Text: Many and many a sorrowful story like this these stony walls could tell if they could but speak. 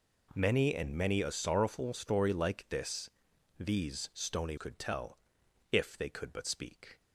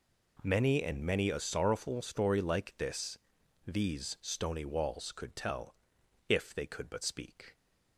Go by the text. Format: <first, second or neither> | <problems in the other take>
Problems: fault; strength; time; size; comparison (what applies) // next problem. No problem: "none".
second | pauses between "this" and "these"; noticeable; at 3.0 s; 0.48 s long; noticeable in the second // skips "walls"; at 4.5 s // pauses between "tell" and "if"; noticeable; at 5.1 s; 0.54 s long; noticeable in the second